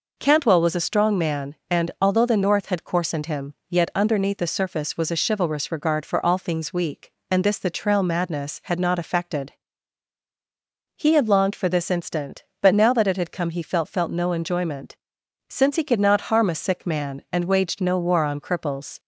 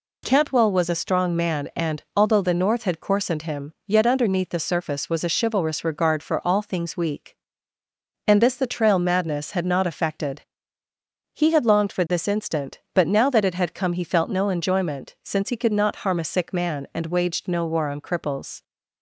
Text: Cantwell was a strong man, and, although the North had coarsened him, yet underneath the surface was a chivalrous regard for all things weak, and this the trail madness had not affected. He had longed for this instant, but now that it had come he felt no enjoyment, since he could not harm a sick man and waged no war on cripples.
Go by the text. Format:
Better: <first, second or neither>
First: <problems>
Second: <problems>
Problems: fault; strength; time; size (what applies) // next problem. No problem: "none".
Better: second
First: says "felt" twice; at 13.8 s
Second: none